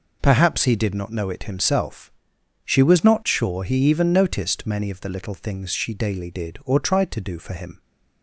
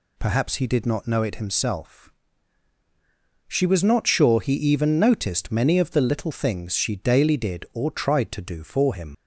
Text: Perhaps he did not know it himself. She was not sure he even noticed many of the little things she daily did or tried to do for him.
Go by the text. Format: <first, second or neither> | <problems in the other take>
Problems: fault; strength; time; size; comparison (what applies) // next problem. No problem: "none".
first | leaves "him" unfinished; at 9.1 s; 70 ms